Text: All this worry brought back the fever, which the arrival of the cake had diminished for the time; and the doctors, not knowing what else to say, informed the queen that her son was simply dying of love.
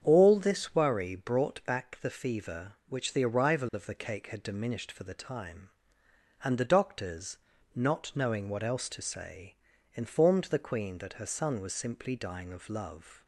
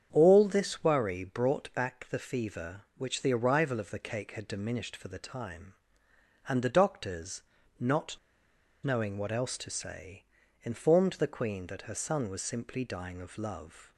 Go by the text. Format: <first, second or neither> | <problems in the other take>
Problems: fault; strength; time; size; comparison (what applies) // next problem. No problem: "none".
first | starts louder than the rest; strong; until 1.1 s; 8 dB; strong in the first // pauses between "not" and "knowing"; noticeable; at 8.1 s; 0.66 s long